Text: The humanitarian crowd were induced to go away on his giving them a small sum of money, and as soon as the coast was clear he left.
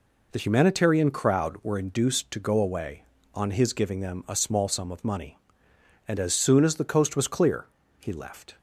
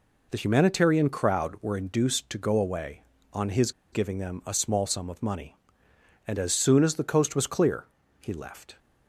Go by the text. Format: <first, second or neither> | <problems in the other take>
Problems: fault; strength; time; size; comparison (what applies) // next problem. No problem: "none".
first | pauses between "his" and "giving"; slight; at 3.7 s; 0.21 s long // pauses between "clear" and "he"; slight; at 7.8 s; 0.34 s long; slight in the first